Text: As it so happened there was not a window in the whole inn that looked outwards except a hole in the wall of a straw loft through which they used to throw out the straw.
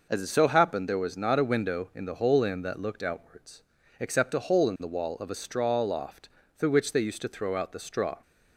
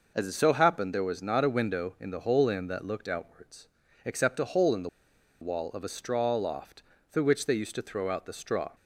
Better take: first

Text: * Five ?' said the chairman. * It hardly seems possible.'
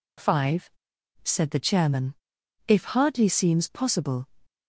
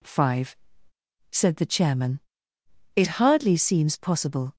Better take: second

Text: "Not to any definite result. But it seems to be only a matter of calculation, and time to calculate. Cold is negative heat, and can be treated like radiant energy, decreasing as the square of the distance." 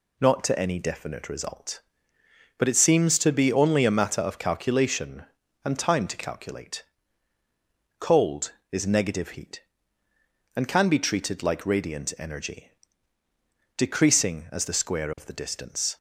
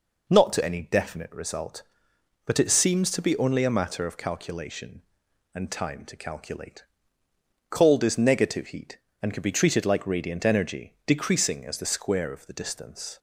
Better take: neither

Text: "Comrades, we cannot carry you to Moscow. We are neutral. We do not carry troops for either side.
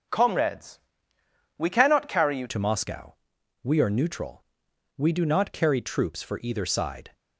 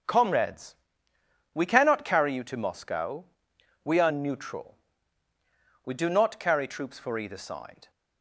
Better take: second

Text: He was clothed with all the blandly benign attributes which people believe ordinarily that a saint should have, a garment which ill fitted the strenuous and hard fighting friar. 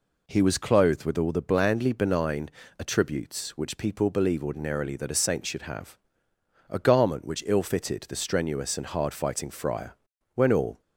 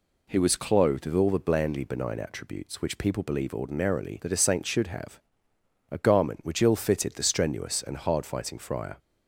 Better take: second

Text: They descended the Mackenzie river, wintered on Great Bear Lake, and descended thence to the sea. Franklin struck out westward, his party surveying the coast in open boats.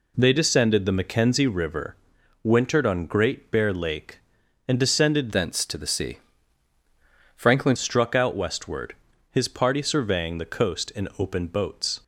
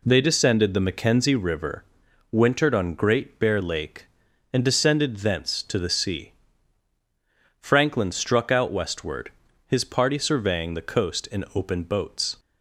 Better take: second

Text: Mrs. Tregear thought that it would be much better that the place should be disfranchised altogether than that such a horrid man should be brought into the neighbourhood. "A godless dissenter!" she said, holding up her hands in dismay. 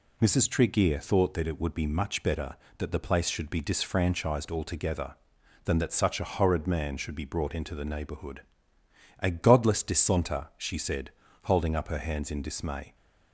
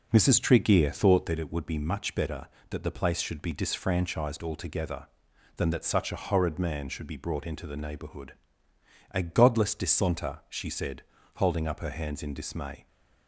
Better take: first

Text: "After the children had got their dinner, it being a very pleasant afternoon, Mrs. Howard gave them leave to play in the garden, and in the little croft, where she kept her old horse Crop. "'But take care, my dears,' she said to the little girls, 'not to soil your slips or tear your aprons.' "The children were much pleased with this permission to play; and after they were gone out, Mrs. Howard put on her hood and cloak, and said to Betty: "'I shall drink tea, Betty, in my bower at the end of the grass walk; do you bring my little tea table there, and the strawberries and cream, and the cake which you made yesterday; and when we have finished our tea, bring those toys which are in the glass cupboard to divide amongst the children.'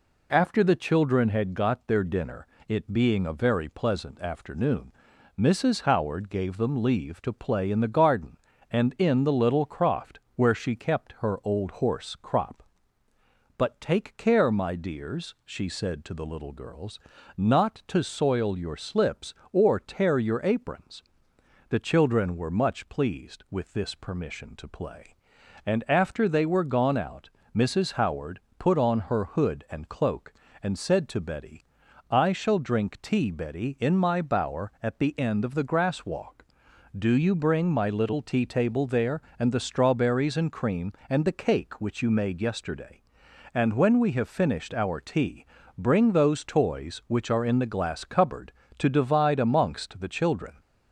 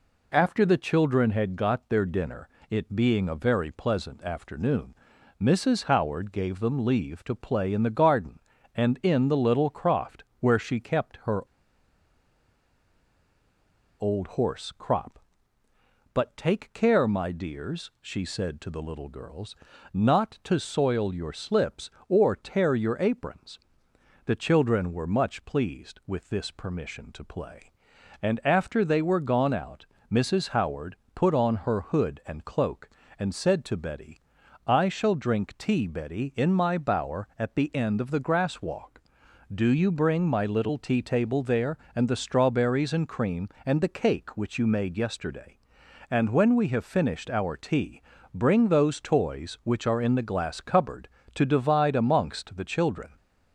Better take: first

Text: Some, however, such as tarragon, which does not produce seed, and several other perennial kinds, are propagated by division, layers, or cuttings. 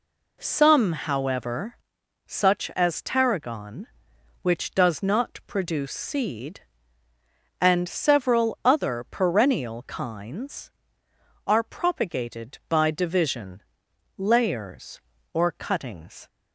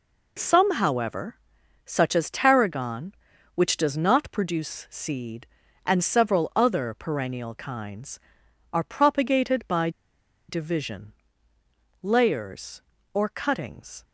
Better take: first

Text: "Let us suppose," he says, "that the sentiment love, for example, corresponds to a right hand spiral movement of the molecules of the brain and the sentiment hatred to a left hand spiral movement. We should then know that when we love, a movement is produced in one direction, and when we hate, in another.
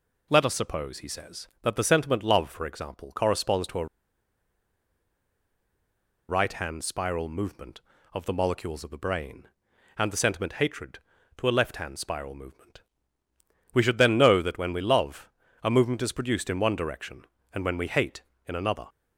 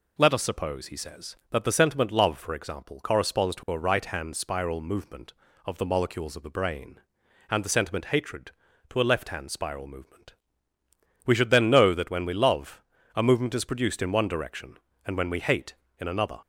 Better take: second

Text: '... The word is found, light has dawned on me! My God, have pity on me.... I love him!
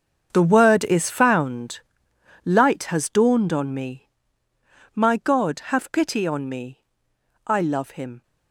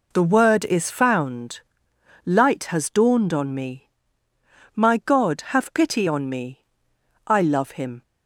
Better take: second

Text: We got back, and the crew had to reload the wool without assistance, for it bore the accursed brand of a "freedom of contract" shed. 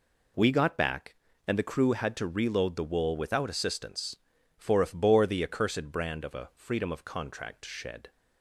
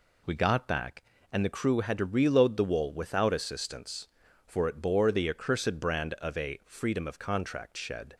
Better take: second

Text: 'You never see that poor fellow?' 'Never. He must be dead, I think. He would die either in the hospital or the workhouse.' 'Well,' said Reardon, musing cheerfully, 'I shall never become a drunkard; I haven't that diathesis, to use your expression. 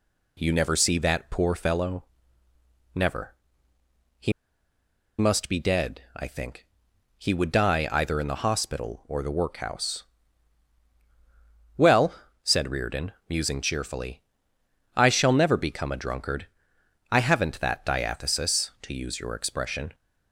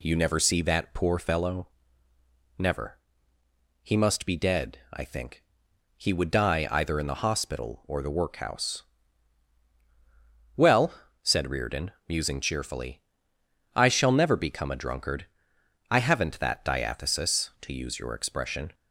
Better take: second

